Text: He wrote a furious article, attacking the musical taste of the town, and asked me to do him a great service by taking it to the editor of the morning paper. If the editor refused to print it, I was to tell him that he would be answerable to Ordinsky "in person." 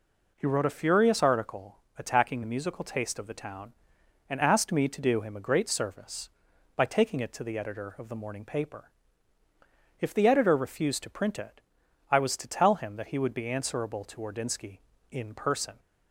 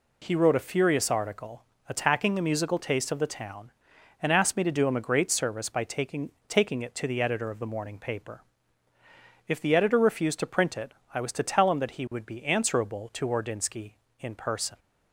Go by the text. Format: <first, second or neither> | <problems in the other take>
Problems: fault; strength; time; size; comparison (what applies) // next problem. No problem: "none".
first | says "taking" twice; at 6.4 s